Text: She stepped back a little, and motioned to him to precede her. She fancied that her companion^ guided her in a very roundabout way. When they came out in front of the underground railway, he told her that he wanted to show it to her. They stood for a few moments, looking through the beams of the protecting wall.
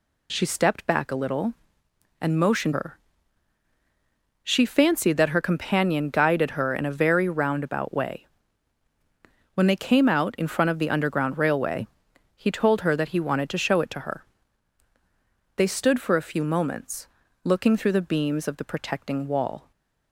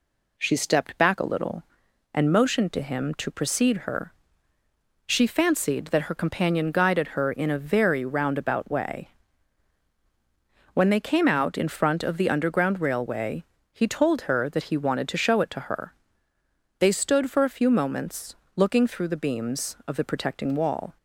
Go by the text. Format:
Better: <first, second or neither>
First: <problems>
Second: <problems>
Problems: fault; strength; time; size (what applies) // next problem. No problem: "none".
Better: second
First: skips "to him to precede"; at 2.7 s // stays silent after the last word; slight; from 19.6 s on; 0.5 s long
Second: none